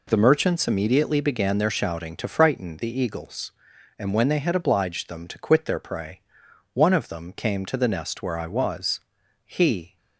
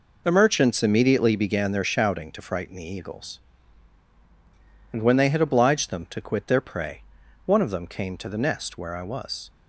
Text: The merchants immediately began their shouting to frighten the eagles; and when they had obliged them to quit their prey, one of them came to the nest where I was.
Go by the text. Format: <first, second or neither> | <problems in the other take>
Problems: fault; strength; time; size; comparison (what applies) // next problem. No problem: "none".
second | goes on to say "He"; from 9.4 s on; 0.52 s long